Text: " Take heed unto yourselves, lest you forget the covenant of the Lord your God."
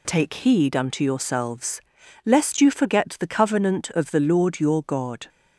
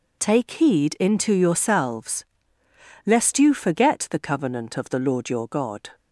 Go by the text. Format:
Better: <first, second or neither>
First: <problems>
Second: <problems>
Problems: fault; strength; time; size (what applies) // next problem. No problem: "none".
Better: first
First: none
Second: says "into" for "unto"; at 0.9 s